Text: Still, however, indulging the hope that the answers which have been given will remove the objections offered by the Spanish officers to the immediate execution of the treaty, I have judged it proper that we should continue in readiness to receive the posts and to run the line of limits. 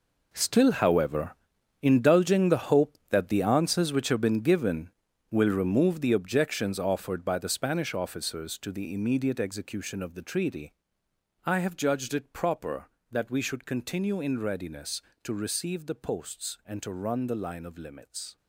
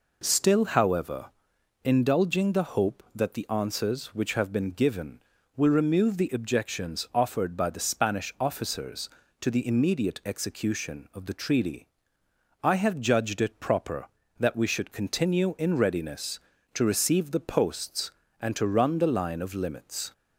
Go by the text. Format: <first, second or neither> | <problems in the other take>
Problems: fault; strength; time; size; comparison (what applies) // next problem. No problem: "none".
second | gets quieter; strong; throughout; 13 dB